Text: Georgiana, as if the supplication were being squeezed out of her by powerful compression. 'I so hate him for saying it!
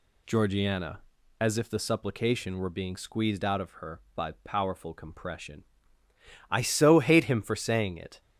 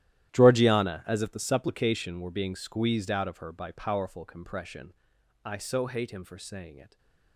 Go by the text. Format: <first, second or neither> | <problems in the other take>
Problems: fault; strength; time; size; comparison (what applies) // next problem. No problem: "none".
first | gets quieter; strong; throughout; 17 dB // stays silent after the last word; slight; from 6.8 s on; 0.5 s long